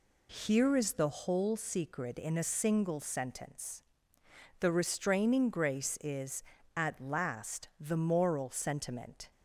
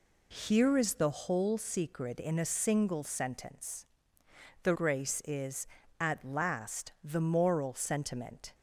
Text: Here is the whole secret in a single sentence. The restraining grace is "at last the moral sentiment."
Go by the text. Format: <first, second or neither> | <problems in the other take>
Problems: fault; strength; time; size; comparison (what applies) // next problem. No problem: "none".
first | skips "restraining"; at 4.7 s